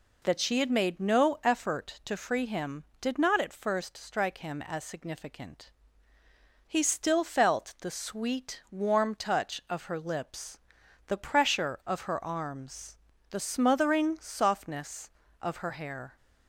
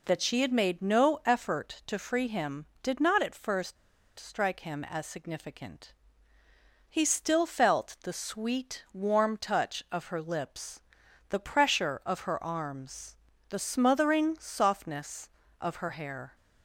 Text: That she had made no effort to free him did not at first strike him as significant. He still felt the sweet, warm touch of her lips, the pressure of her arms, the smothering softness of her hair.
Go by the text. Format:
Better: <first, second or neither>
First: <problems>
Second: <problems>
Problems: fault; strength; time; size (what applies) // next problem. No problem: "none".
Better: first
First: none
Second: pauses between "first" and "strike"; at 3.7 s; 0.42 s long